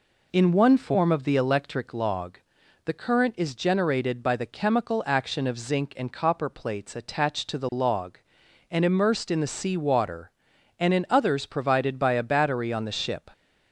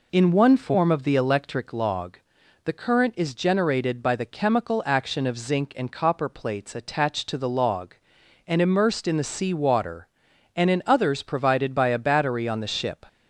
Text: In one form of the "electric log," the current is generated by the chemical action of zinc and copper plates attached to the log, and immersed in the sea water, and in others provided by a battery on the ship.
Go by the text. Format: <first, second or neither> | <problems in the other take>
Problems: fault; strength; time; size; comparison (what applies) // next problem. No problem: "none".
neither | none